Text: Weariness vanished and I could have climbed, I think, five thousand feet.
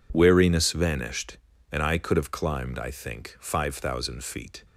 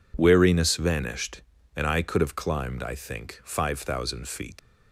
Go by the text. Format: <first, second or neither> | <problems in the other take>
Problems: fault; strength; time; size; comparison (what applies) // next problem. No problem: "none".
first | leaves "feet" unfinished; at 4.5 s; 100 ms